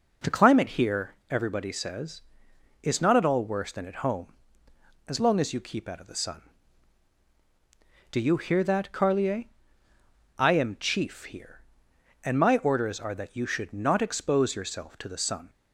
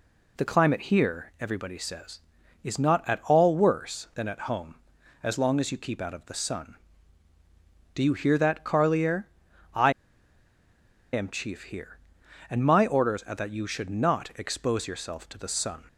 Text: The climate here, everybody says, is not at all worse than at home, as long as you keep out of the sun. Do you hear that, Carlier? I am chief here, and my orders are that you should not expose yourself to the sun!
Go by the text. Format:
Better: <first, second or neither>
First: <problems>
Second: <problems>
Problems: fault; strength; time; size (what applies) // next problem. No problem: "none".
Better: first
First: none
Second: pauses between "I" and "am"; at 9.9 s; 1.2 s long